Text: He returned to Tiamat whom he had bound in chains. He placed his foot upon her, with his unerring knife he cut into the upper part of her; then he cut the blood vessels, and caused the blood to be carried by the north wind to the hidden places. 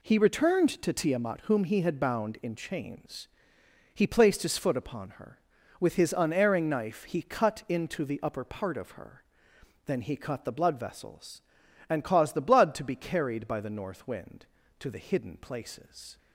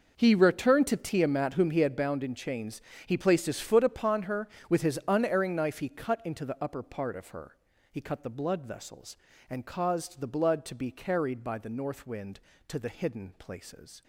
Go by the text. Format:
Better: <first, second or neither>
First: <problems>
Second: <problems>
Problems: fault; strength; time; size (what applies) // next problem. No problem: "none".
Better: first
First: none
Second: skips "then"; at 7.7 s